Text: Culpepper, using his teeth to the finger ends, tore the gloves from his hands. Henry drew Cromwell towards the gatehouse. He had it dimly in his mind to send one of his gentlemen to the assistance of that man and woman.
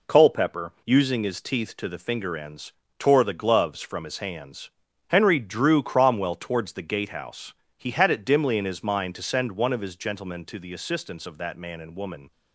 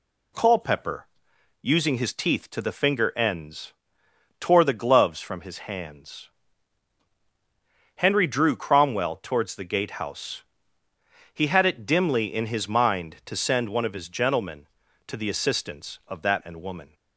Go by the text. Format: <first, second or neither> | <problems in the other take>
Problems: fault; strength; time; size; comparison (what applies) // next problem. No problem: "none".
first | skips "man"; at 16.4 s